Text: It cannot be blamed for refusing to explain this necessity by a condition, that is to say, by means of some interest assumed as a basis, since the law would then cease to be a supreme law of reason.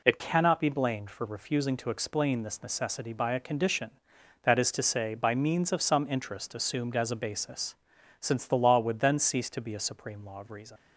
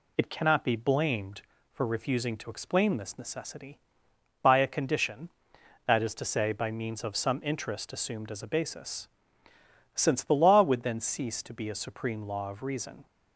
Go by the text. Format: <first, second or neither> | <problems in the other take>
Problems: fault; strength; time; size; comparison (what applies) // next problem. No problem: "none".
second | leaves "reason" unfinished; at 10.7 s; 110 ms